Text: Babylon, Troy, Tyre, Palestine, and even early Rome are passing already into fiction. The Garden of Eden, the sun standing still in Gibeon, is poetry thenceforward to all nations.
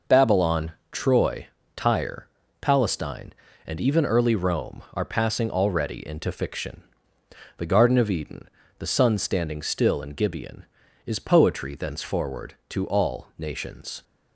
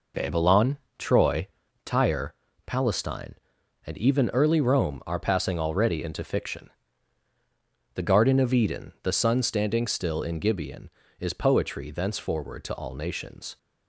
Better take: neither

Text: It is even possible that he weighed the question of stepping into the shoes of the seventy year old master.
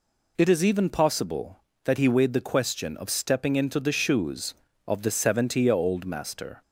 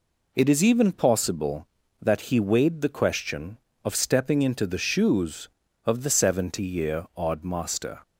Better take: first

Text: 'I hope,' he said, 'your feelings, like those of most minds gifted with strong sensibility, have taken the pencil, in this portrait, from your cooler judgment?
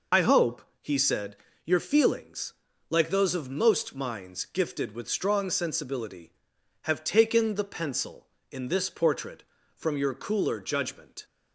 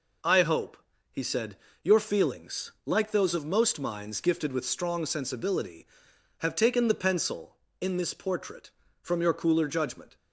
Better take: second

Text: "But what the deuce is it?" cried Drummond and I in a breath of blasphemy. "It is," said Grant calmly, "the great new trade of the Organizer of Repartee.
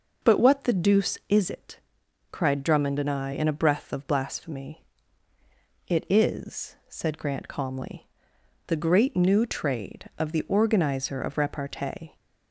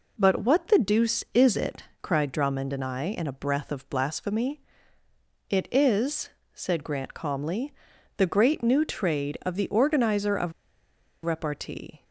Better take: first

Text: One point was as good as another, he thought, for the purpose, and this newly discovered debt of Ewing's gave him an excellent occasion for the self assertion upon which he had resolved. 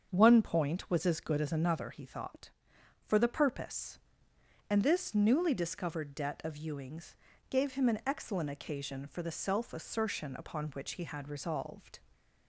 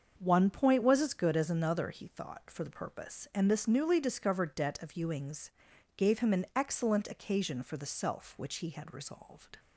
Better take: first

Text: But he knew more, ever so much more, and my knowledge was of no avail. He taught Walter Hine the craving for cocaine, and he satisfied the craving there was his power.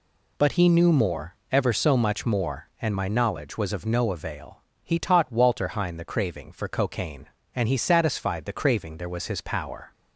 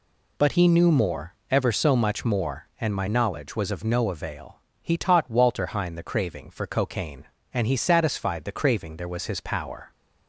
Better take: neither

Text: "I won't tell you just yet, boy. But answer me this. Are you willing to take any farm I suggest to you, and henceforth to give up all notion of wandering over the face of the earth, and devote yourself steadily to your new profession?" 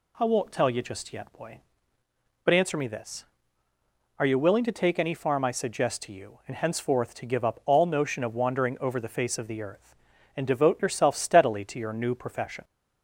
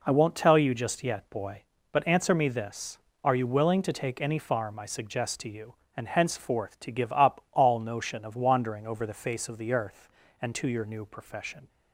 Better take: first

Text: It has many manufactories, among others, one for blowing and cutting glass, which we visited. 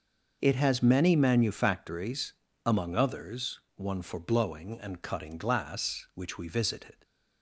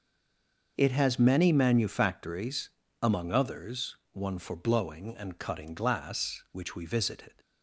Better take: first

